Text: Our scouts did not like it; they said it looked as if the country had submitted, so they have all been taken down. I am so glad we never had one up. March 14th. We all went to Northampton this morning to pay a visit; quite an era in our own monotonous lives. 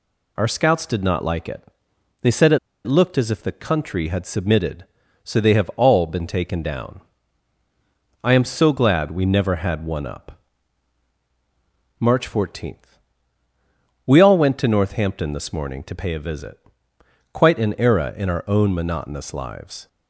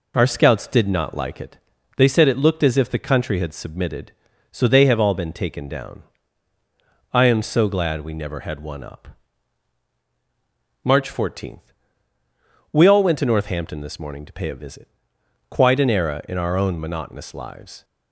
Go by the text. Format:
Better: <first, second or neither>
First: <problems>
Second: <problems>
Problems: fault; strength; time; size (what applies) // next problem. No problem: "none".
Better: second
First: pauses between "it" and "looked"; slight; at 2.5 s; 0.26 s long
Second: none